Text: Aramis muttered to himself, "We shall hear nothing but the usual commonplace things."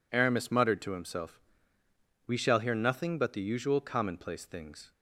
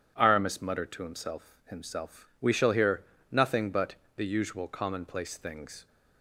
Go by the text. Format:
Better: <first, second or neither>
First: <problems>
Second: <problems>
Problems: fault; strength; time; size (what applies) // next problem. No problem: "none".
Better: first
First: none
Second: says "himself" twice; at 1.7 s // pauses between "hear" and "nothing"; slight; at 3.0 s; 0.28 s long // pauses between "but" and "the"; slight; at 3.9 s; 0.22 s long